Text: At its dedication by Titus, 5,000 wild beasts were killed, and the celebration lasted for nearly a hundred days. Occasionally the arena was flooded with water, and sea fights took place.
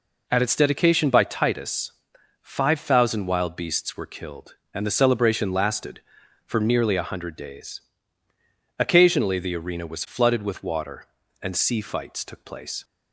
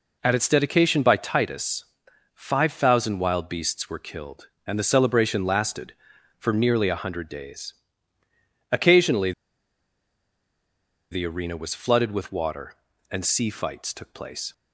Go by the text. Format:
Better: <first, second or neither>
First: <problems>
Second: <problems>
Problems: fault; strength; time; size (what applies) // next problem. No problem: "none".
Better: first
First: none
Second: pauses between "Occasionally" and "the"; strong; at 9.3 s; 1.8 s long